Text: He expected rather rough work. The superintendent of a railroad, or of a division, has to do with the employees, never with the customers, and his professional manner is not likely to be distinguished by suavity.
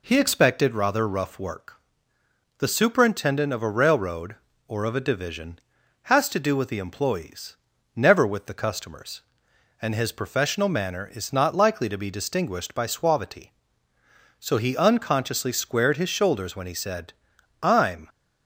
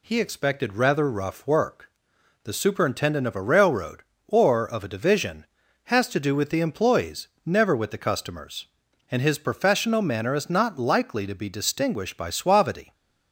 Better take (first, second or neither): second